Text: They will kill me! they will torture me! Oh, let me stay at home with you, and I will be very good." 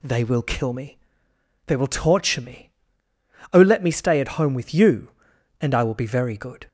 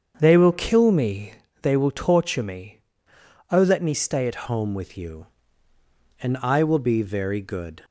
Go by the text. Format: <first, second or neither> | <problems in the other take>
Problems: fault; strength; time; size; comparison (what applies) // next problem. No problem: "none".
first | starts louder than the rest; strong; until 1.2 s; 7.5 dB // changes voice at "home"; from 4.4 s on; 3.4 s long